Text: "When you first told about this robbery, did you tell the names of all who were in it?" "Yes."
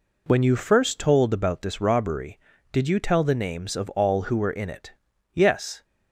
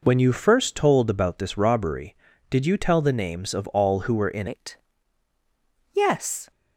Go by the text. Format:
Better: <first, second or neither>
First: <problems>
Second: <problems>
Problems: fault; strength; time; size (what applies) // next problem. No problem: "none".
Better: first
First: none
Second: changes voice at "it"; from 4.4 s on; 2.1 s long